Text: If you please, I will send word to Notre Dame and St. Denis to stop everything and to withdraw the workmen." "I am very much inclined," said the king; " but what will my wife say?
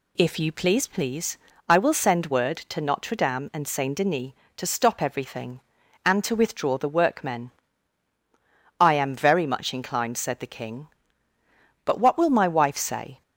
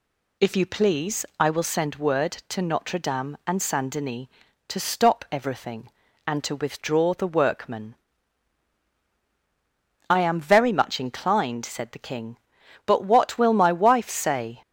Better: second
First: says "please" twice; at 0.8 s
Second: none

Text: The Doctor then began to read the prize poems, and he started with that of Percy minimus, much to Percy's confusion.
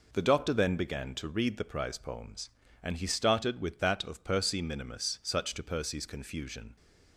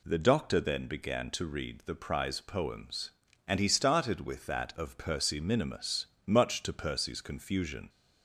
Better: second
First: says "such" for "much"; at 5.2 s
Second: none

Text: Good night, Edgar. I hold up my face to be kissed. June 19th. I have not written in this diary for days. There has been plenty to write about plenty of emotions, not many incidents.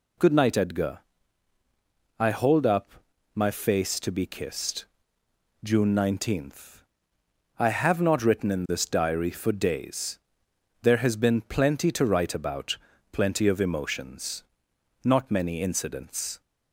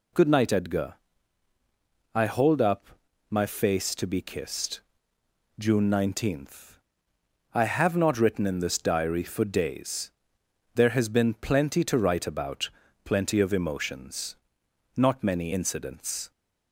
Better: neither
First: pauses between "up" and "my"; at 2.9 s; 0.42 s long // pauses between "about" and "plenty"; slight; at 12.7 s; 0.36 s long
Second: pauses between "up" and "my"; at 2.8 s; 0.42 s long // pauses between "about" and "plenty"; slight; at 12.6 s; 0.36 s long

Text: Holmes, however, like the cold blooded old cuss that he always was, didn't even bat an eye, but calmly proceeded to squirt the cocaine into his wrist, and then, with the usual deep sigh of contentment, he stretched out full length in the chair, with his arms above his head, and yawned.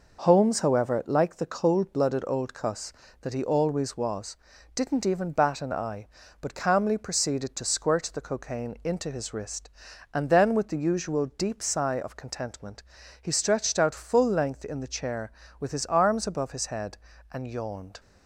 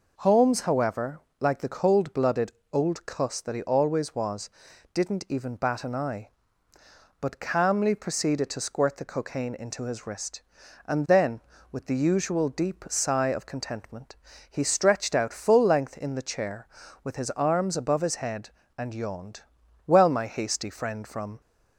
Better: first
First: none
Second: pauses between "blooded" and "old"; slight; at 2.5 s; 0.20 s long // goes on to say "Well my hasty friend from"; from 19.8 s on; 1.5 s long

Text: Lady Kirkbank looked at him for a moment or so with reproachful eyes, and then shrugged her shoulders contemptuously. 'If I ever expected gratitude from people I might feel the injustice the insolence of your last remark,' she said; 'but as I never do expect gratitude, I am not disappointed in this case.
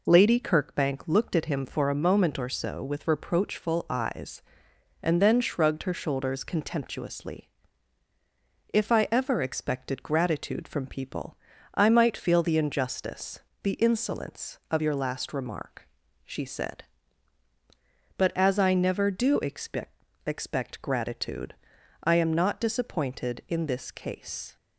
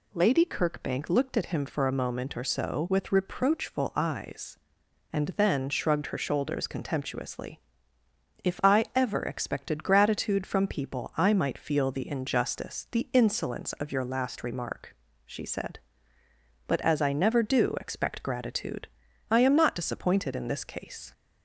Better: second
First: pauses between "people" and "I"; slight; at 11.3 s; 0.36 s long // pauses between "injustice" and "the"; slight; at 13.3 s; 0.24 s long // says "expect" twice; at 20.2 s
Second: none

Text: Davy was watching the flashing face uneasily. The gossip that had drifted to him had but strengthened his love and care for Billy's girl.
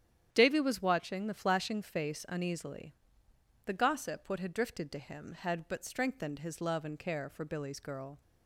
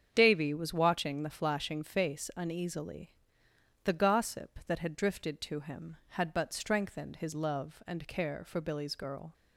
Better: second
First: starts louder than the rest; strong; until 1.3 s; 9.5 dB // says "what" for "that"; at 4.2 s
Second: starts louder than the rest; strong; until 1.1 s; 8 dB

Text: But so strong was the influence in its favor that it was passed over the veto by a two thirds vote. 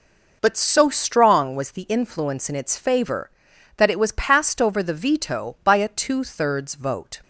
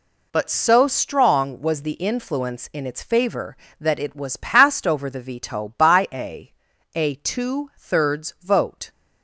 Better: first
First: none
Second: says "a" twice; at 6.9 s

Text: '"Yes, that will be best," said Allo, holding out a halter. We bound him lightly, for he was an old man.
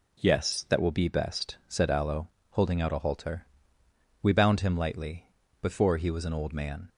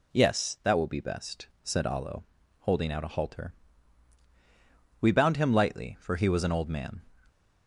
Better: second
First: says "before" for "for"; at 5.6 s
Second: none

